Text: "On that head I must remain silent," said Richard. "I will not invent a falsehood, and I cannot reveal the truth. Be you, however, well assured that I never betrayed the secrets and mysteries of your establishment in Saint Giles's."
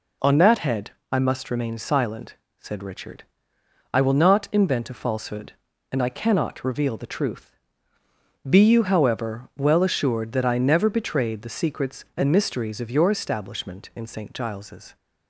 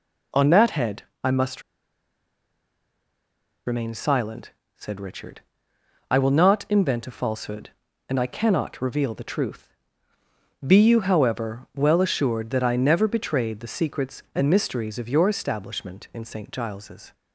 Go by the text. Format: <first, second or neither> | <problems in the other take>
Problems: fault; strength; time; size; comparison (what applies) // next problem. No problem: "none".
first | pauses between "head" and "I"; slight; at 1.0 s; 0.20 s long; slight in the first // pauses between "must" and "remain"; strong; at 1.6 s; 2.0 s long